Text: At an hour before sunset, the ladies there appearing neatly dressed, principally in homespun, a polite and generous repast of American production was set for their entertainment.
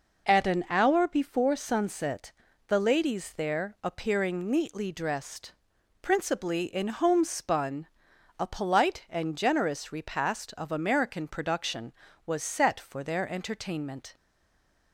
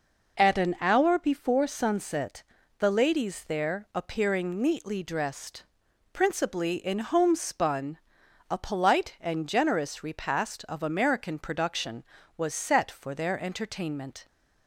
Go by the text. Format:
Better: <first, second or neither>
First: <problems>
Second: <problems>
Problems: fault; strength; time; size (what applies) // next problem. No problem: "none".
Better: second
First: stays silent after the last word; slight; from 14.1 s on; 0.8 s long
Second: none